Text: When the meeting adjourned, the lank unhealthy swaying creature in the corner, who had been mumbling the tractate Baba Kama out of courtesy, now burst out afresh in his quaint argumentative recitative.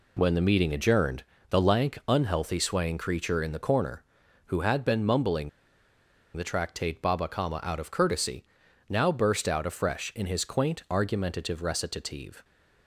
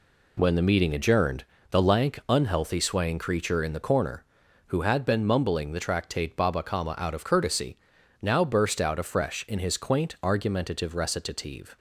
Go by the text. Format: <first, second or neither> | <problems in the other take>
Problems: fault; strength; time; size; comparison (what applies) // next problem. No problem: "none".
second | pauses between "mumbling" and "the"; noticeable; at 5.4 s; 0.86 s long